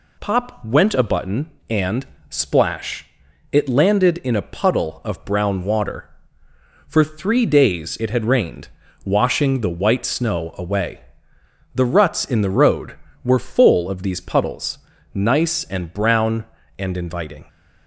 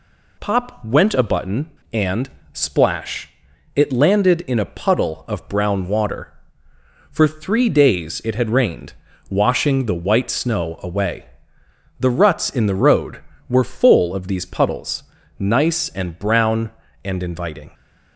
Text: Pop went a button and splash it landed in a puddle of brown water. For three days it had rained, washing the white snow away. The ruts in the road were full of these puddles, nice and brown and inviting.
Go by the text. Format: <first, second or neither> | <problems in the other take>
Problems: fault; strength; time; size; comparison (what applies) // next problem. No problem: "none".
neither | pauses between "and" and "splash"; slight; the same in both // pauses between "splash" and "it"; noticeable; the same in both